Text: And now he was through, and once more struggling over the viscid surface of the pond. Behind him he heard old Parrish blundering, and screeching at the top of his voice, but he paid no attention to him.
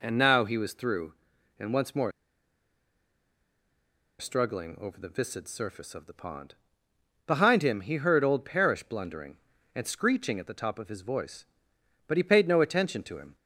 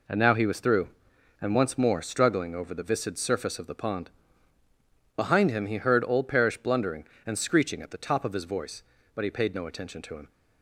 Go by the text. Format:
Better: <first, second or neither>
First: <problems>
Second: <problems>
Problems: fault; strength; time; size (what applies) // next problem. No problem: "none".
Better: second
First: pauses between "more" and "struggling"; strong; at 2.1 s; 2.0 s long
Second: none